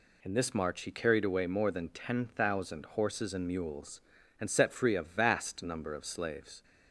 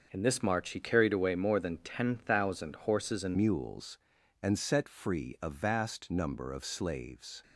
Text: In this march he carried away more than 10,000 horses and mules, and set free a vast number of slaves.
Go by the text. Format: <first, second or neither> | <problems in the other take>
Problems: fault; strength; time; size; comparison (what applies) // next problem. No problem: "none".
first | starts louder than the rest; noticeable; until 1.1 s; 6 dB // changes voice at "mules"; from 3.3 s on; 4.1 s long